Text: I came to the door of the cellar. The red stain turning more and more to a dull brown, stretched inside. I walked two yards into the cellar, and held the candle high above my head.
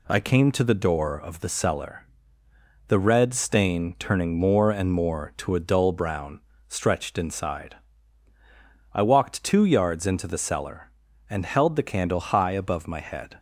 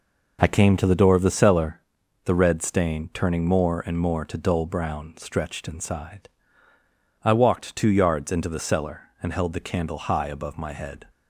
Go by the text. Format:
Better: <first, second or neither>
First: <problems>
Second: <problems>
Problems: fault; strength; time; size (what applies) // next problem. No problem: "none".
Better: first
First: none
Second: skips "a"; at 4.3 s